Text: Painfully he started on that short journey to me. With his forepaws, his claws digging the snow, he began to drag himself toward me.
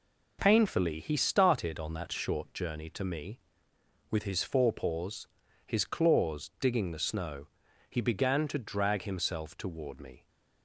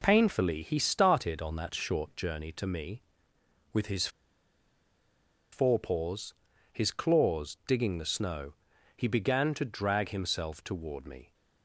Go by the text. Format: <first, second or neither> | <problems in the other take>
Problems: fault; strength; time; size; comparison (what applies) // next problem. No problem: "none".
first | pauses between "his" and "forepaws"; strong; at 4.0 s; 1.4 s long